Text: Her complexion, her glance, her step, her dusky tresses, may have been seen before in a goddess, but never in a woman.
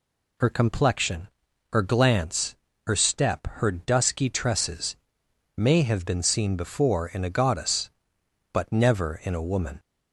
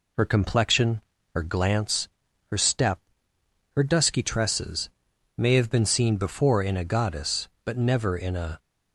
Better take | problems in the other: first | stops before "woman"; at 8.5 s

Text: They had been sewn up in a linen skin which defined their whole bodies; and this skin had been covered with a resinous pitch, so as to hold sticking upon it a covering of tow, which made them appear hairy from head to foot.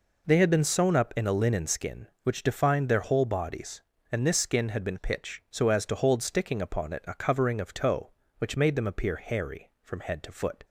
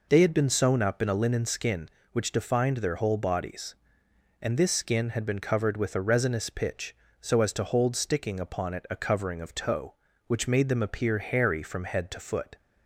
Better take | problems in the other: second | skips "covered with a resinous"; at 4.9 s

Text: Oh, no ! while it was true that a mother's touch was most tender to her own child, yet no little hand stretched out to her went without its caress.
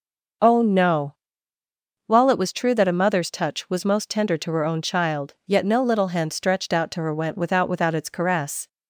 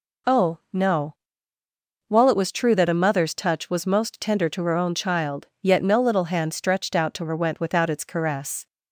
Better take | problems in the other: second | starts louder than the rest; noticeable; until 2.3 s; 6 dB // says "without" twice; at 7.6 s

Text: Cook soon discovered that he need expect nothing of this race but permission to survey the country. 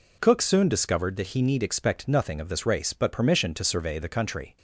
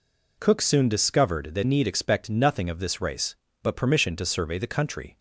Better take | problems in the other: first | skips "he"; at 1.6 s

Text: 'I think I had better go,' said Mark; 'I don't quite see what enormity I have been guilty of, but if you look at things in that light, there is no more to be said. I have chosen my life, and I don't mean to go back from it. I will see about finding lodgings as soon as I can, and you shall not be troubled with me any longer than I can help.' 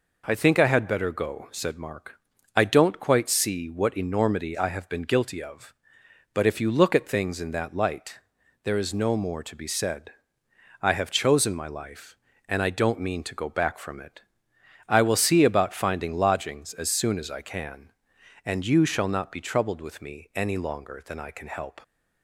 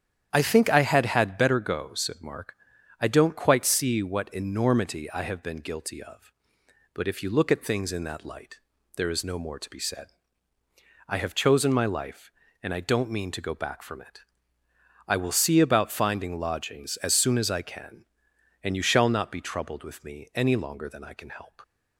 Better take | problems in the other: first | starts louder than the rest; strong; until 1.3 s; 9.5 dB // says "had" twice; at 1.0 s

